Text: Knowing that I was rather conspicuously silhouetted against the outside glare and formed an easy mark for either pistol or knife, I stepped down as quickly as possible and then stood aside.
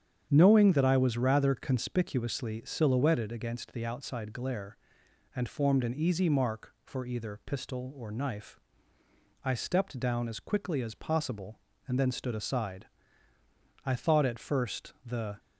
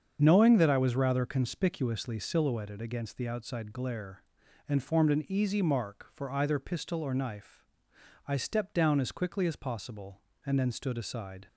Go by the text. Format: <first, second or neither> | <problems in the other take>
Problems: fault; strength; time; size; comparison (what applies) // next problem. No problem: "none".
second | starts louder than the rest; strong; until 1.3 s; 8.5 dB; strong in the second // goes on to say "I thought at first the"; from 13.8 s on; 1.5 s long